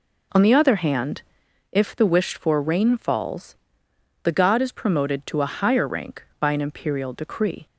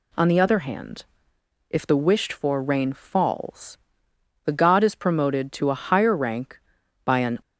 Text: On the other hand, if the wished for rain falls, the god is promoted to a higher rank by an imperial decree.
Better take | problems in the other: first | stops before "imperial decree"; at 7.4 s

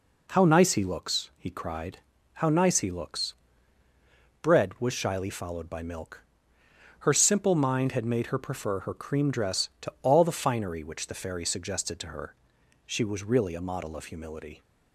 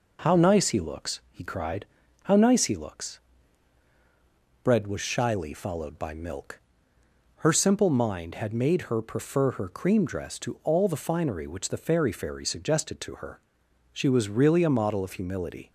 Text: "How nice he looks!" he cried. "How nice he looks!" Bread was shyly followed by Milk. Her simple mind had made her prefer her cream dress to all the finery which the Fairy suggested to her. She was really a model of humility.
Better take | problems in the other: first | says "Fairy" twice; at 12.1 s

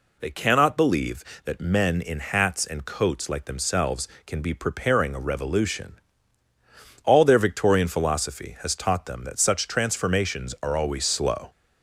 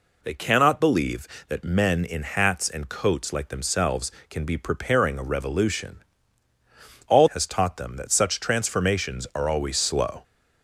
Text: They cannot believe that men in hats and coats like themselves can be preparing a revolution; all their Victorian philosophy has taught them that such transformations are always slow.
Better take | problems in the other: first | skips "their Victorian philosophy"; at 7.3 s

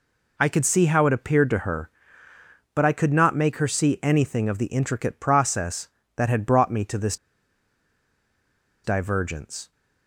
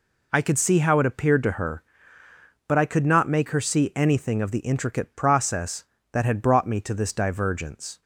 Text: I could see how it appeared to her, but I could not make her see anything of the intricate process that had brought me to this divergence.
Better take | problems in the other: second | pauses between "this" and "divergence"; strong; at 7.1 s; 1.6 s long

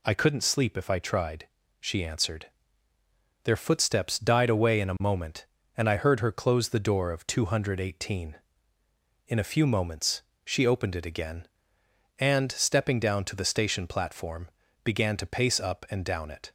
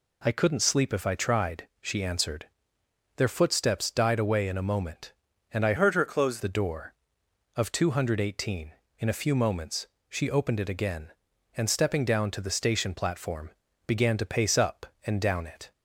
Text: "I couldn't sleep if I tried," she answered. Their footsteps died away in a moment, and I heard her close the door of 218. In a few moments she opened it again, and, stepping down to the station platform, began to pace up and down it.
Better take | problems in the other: first | changes voice from "heard" to "close"; from 5.7 to 6.3 s; 0.6 s long // pauses between "moments" and "she"; slight; at 9.8 s; 0.22 s long; slight in the first

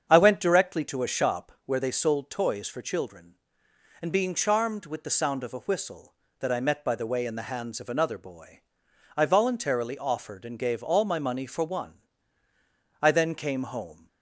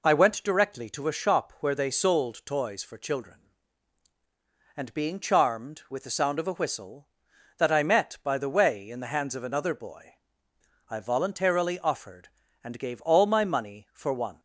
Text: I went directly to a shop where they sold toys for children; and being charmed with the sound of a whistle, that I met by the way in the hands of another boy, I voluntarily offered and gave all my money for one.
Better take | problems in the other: second | starts louder than the rest; strong; until 1.1 s; 7.5 dB // goes on to say "I then came home"; noticeable; from 13.0 s on; 1.0 s long

